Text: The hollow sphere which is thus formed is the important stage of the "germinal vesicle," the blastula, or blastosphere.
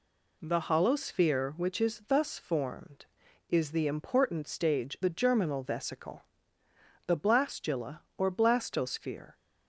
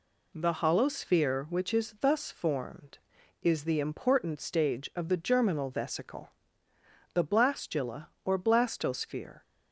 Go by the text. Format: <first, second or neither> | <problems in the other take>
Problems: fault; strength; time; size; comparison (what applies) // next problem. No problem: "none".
second | skips "of"; at 4.9 s